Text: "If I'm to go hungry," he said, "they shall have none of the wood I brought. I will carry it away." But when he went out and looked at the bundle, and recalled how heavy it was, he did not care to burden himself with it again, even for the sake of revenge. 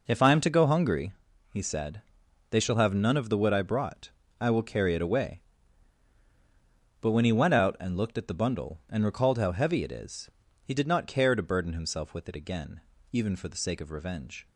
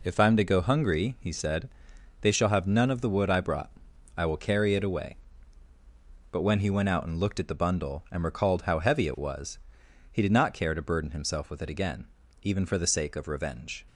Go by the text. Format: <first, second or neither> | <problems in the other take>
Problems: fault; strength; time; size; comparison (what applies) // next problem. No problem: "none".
second | says "is" for "was"; at 9.9 s